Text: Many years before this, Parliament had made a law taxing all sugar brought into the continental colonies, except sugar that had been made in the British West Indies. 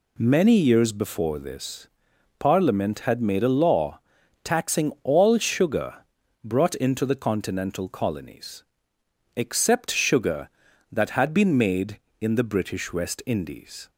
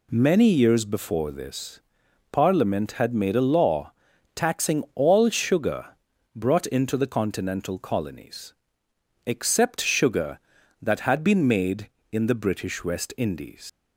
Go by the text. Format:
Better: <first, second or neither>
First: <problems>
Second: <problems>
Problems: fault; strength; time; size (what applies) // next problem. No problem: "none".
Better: first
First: pauses between "law" and "taxing"; at 3.9 s; 0.44 s long // pauses between "sugar" and "brought"; noticeable; at 5.9 s; 0.50 s long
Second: pauses between "law" and "taxing"; at 3.9 s; 0.42 s long // pauses between "sugar" and "brought"; noticeable; at 5.8 s; 0.50 s long // leaves "Indies" unfinished; at 13.6 s; 115 ms